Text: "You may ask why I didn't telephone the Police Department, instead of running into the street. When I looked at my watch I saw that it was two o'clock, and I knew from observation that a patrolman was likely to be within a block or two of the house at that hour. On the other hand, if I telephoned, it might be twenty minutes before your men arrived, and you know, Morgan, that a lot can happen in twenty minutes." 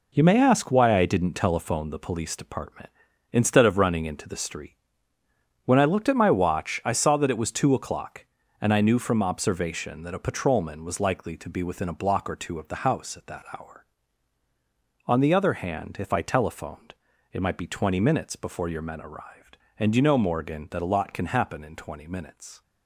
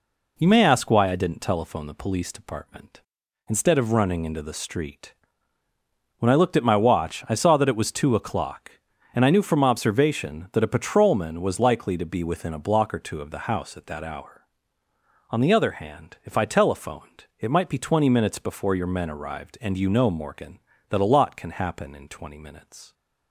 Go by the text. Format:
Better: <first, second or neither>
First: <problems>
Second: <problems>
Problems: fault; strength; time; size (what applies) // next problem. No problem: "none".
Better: second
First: gets quieter; strong; throughout; 8.5 dB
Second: none